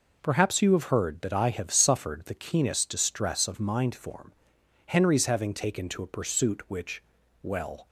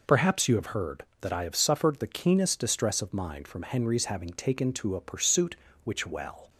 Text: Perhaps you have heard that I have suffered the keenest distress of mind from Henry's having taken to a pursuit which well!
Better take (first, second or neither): second